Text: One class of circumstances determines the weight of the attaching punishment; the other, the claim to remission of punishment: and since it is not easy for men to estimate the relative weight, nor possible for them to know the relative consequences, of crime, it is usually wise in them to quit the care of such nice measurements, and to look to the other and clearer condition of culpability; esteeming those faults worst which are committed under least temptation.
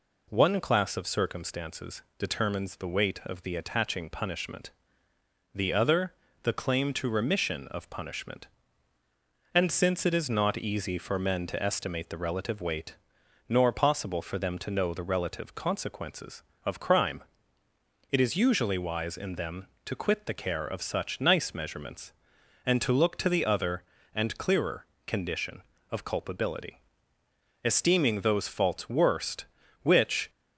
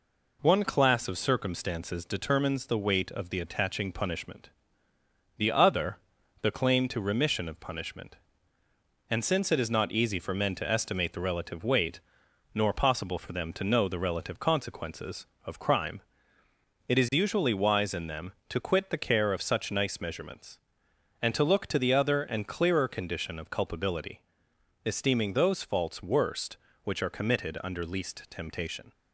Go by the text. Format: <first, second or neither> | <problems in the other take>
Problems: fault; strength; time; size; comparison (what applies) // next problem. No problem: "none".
second | pauses between "circumstances" and "determines"; slight; at 2.0 s; 0.16 s long // pauses between "clearer" and "condition"; slight; at 24.8 s; 0.20 s long // stops before "are committed under least temptation"; at 30.2 s